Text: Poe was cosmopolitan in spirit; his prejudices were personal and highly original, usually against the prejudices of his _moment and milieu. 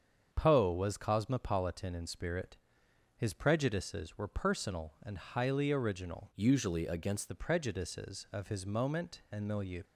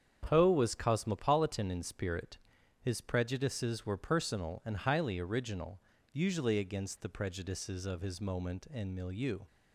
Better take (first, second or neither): second